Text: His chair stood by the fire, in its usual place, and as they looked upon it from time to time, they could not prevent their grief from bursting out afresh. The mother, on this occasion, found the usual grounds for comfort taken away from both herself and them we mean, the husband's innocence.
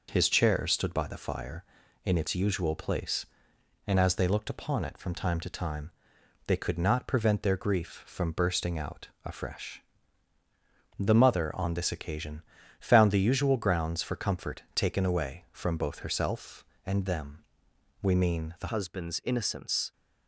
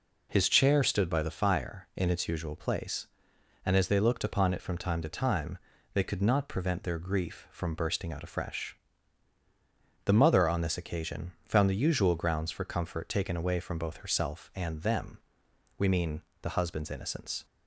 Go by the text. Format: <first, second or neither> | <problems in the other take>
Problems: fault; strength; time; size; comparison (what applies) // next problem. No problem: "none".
second | pauses between "them" and "we"; noticeable; at 17.4 s; 0.58 s long; noticeable in the second // changes voice at "husband's"; from 18.6 s on; 1.3 s long